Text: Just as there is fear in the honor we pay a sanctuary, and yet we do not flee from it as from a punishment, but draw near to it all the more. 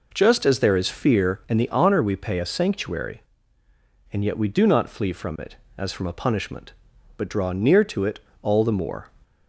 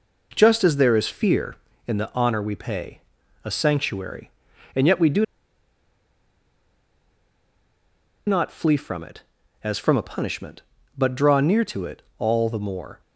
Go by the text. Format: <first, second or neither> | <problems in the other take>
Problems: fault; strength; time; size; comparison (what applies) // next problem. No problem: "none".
first | pauses between "pay" and "a"; at 3.0 s; 0.44 s long // pauses between "do" and "not"; strong; at 5.2 s; 3.0 s long // pauses between "it" and "all"; slight; at 12.0 s; 0.16 s long; slight in the first